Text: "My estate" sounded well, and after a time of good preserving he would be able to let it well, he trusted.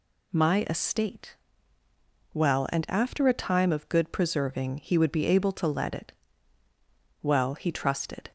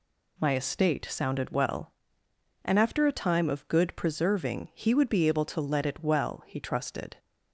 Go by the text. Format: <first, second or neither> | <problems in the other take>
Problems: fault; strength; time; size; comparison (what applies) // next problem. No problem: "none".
second | skips "sounded"; at 1.8 s // pauses between "it" and "well"; at 6.1 s; 1.0 s long